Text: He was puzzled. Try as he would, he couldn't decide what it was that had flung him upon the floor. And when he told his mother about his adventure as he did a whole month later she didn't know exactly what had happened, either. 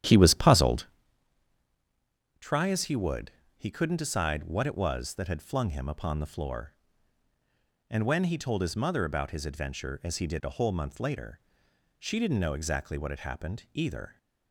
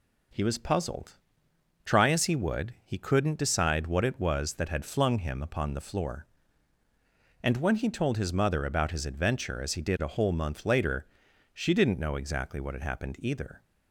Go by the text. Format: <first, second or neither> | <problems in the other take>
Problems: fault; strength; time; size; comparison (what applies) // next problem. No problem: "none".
second | starts louder than the rest; strong; until 1.1 s; 10.5 dB // pauses between "later" and "she"; noticeable; at 11.3 s; 0.60 s long; noticeable in the second